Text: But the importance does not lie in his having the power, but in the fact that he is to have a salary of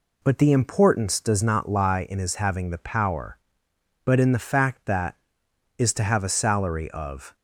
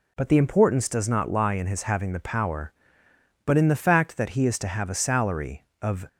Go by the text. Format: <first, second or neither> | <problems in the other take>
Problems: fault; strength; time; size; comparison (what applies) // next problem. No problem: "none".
second | skips "he"; at 5.4 s